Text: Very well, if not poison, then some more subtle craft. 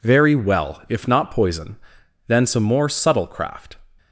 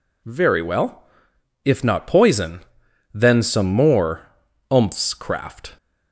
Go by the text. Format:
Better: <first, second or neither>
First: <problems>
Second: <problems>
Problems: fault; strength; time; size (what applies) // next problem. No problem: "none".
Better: first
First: none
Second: says "umphs" for "subtle"; at 4.7 s